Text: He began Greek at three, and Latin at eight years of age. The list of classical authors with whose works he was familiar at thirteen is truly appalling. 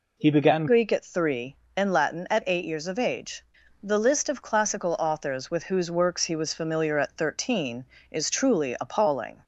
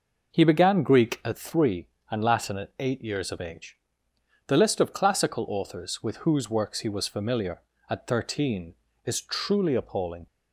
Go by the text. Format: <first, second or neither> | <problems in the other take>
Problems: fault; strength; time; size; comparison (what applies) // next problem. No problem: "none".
second | changes voice at "Greek"; from 0.6 s on; 8.8 s long